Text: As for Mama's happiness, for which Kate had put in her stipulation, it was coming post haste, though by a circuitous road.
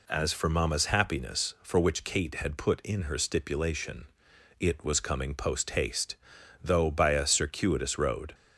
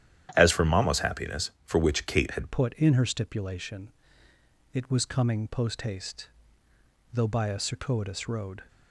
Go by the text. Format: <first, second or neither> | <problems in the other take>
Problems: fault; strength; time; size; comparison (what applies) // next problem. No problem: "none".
first | starts louder than the rest; strong; until 1.3 s; 11 dB // changes voice at "put"; from 2.5 s on; 6.1 s long